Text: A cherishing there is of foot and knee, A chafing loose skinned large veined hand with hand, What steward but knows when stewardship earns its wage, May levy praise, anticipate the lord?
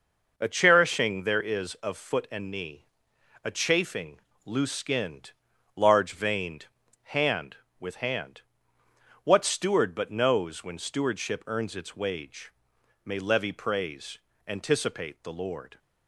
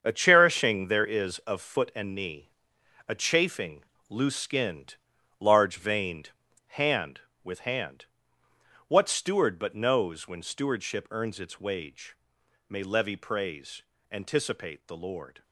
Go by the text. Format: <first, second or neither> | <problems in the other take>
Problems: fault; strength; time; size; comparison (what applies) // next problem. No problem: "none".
first | gets quieter; strong; throughout; 9.5 dB // pauses between "chafing" and "loose"; slight; at 3.8 s; 0.24 s long; slight in the first // pauses between "skinned" and "large"; noticeable; at 4.9 s; 0.46 s long; noticeable in the first // pauses between "veined" and "hand"; at 6.3 s; 0.38 s long; also in the first